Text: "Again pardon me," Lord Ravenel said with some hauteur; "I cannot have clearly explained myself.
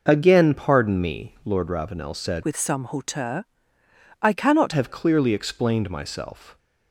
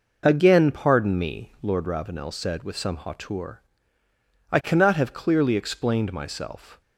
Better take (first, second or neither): second